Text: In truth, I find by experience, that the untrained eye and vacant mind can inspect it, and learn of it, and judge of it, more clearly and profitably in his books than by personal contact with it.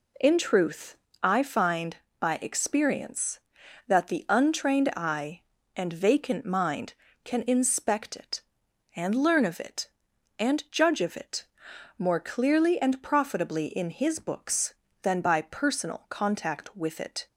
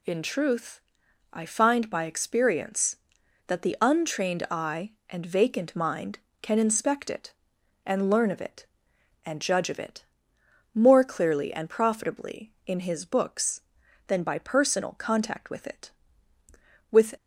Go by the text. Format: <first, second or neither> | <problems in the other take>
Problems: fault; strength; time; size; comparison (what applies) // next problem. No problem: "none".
first | goes on to say "With"; slight; from 16.9 s on; 0.24 s long